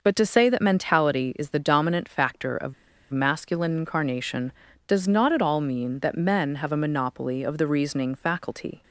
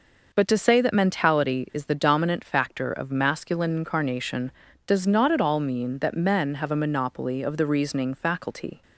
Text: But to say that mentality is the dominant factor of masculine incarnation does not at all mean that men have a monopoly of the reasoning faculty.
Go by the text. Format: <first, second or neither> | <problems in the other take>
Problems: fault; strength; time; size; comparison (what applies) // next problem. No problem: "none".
second | pauses between "of" and "masculine"; at 2.7 s; 0.36 s long